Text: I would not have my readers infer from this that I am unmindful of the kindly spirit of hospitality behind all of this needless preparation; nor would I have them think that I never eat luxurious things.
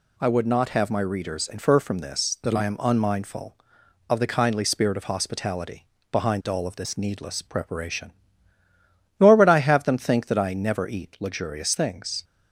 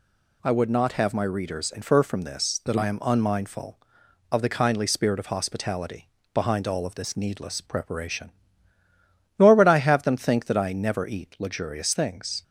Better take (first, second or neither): neither